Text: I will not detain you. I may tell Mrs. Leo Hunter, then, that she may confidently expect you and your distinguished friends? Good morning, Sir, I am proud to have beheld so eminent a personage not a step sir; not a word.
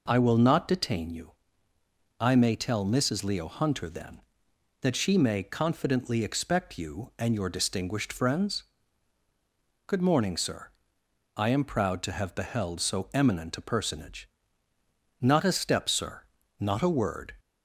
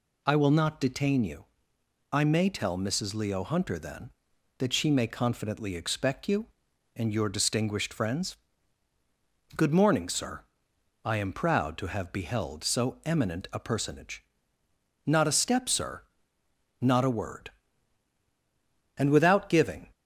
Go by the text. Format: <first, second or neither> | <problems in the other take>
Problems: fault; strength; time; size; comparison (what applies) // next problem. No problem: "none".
first | pauses between "personage" and "not"; noticeable; at 14.2 s; 0.80 s long; noticeable in the first // goes on to say "And without giving"; noticeable; from 18.9 s on; 0.96 s long